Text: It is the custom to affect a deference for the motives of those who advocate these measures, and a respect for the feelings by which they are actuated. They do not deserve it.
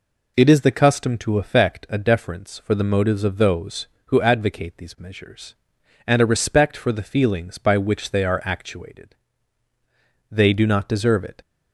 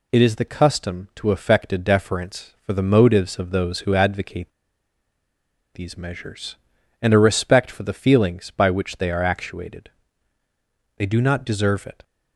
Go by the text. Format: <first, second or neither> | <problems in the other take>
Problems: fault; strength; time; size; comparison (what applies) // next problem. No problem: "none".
first | pauses between "advocate" and "these"; at 4.5 s; 1.2 s long